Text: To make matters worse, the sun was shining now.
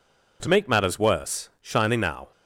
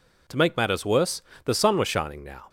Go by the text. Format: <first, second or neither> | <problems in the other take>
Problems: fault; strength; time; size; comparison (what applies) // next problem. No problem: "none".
second | skips "the sun was"; at 1.5 s